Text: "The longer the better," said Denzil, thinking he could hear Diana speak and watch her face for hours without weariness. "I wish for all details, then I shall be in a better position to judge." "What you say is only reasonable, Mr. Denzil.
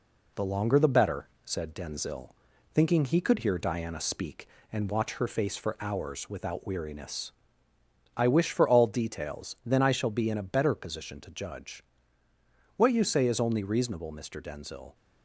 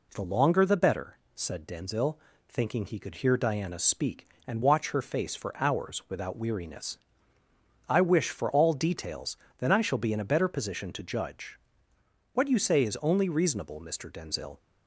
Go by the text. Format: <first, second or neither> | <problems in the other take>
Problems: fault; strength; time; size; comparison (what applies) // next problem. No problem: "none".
second | gets quieter; slight; throughout; 2.5 dB